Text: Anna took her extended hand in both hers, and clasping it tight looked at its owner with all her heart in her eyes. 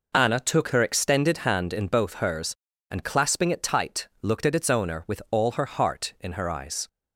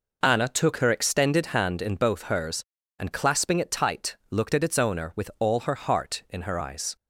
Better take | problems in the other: neither | none

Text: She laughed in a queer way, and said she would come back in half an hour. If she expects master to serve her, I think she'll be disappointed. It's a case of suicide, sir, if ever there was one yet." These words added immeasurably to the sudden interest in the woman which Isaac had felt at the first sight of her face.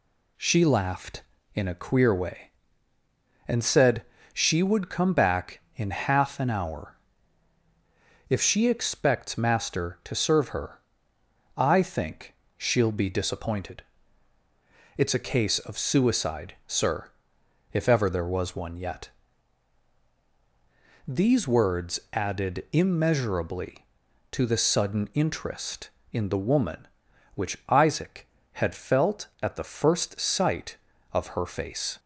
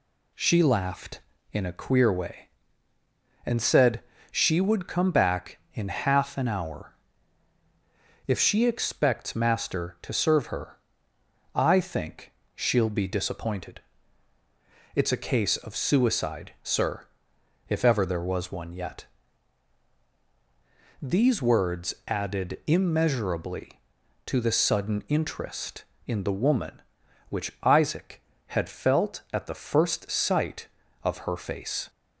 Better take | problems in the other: neither | pauses between "said" and "she"; slight; the same in both // pauses between "think" and "she'll"; slight; the same in both

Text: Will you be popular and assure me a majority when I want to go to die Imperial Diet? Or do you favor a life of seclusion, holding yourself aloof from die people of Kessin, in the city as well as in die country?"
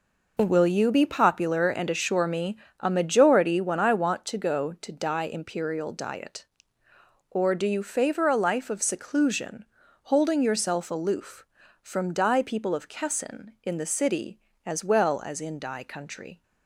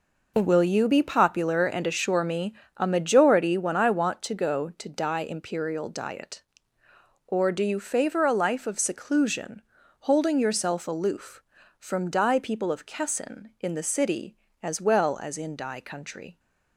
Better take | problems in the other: neither | pauses between "me" and "a"; slight; the same in both

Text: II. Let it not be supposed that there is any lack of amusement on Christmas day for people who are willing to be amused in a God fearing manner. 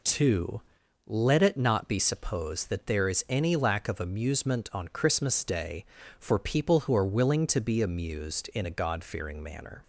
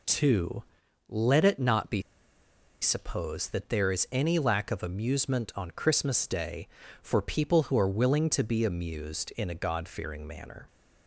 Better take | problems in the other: first | pauses between "be" and "supposed"; noticeable; at 2.0 s; 0.80 s long

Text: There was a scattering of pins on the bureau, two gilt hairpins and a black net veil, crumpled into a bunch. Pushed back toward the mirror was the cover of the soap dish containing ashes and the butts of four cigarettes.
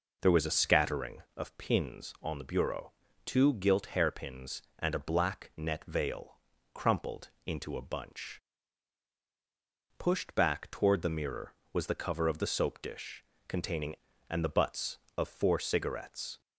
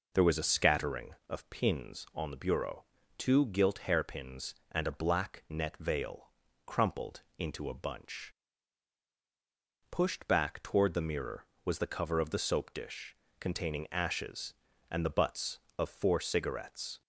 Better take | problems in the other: second | pauses between "crumpled" and "into"; slight; at 7.2 s; 0.16 s long; slight in the second // pauses between "dish" and "containing"; slight; at 13.2 s; 0.24 s long; slight in the second // skips "ashes"; at 14.1 s

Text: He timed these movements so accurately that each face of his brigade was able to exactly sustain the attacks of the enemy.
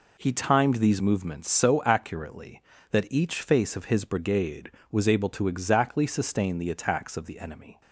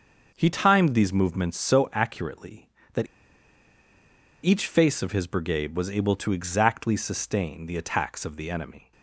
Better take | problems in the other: first | starts louder than the rest; until 1.3 s; 6 dB // pauses between "that" and "each"; strong; at 3.0 s; 1.3 s long

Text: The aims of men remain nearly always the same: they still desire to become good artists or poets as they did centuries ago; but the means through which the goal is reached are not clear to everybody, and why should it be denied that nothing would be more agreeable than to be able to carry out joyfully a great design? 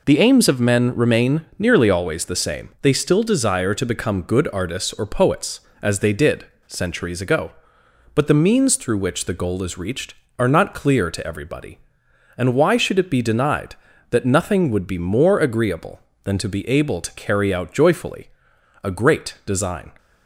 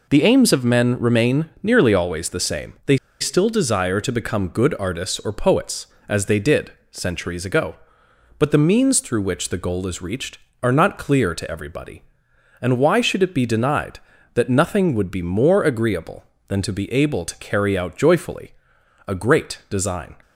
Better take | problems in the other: first | pauses between "they" and "still"; slight; at 2.9 s; 0.24 s long // pauses between "did" and "centuries"; slight; at 6.6 s; 0.22 s long; slight in the first // pauses between "joyfully" and "a"; noticeable; at 18.5 s; 0.56 s long; noticeable in the first

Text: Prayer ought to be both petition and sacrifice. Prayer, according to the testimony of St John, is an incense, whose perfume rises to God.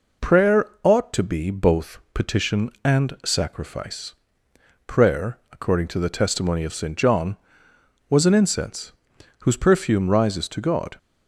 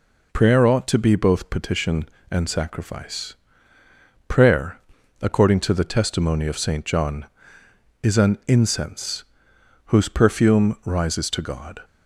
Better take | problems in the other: second | pauses between "both" and "petition"; slight; at 1.9 s; 0.16 s long // says "was" for "is"; at 8.0 s

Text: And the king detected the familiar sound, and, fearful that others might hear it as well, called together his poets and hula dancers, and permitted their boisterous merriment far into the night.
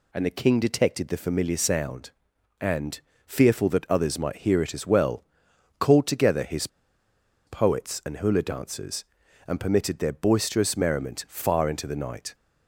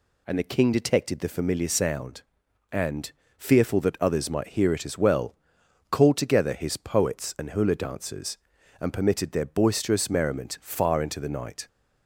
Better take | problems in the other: second | pauses between "his" and "poets"; noticeable; at 6.6 s; 0.79 s long

